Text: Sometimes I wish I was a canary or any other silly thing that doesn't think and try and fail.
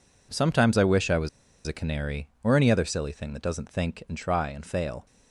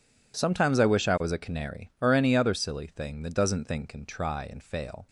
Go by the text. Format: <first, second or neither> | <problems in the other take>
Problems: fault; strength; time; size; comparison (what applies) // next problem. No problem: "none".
second | pauses between "was" and "a"; at 1.2 s; 0.38 s long